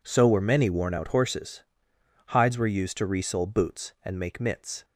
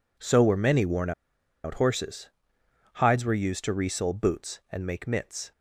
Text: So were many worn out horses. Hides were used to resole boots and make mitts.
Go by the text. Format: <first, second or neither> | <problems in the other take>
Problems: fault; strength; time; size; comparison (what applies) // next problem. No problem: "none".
first | pauses between "worn" and "out"; noticeable; at 1.1 s; 0.53 s long